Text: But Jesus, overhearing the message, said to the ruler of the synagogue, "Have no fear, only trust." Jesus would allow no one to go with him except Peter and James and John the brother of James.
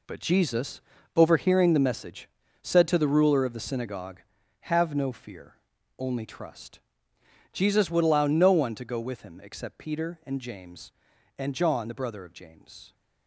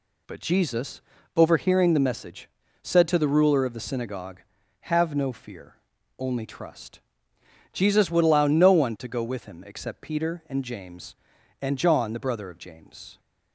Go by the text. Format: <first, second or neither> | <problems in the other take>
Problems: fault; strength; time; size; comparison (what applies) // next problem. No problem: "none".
second | gets quieter; strong; throughout; 11 dB